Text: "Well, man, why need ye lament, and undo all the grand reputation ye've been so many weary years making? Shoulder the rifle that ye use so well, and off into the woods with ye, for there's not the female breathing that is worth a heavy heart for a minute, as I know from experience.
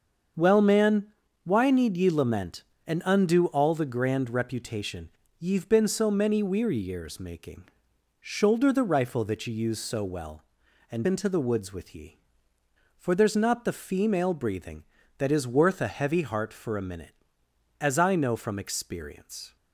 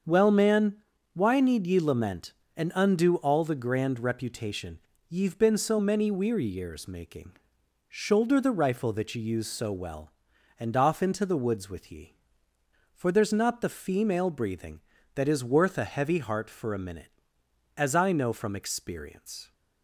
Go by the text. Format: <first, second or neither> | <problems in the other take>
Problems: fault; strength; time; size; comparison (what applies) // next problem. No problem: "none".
second | starts louder than the rest; until 1.6 s; 6.5 dB; also in the second // pauses between "reputation" and "ye've"; slight; at 5.0 s; 0.28 s long; slight in the second // skips "off"; at 11.0 s